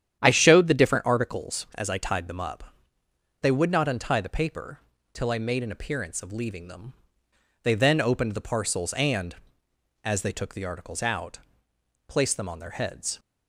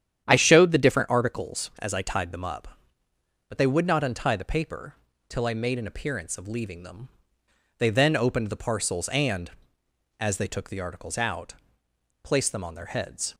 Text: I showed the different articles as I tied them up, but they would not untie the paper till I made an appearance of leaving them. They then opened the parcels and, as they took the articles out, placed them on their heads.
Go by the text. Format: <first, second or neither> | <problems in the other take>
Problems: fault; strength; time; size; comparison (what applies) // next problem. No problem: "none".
second | starts louder than the rest; strong; until 1.2 s; 9.5 dB; strong in the second // skips "but"; at 3.0 s // pauses between "paper" and "till"; slight; at 4.7 s; 0.34 s long; slight in the second